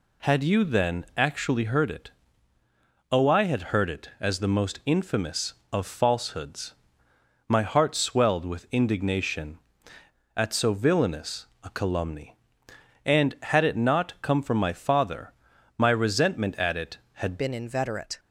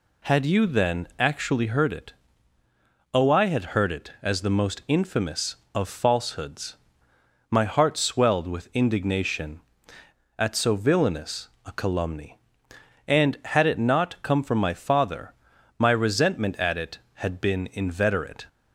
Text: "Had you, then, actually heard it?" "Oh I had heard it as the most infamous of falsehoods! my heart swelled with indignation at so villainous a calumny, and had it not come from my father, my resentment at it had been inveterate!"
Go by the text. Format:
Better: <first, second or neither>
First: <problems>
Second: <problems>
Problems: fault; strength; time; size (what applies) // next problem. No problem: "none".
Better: second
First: pauses between "villainous" and "a"; slight; at 11.4 s; 0.18 s long // changes voice at "been"; from 17.3 s on; 0.8 s long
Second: pauses between "villainous" and "a"; slight; at 11.4 s; 0.18 s long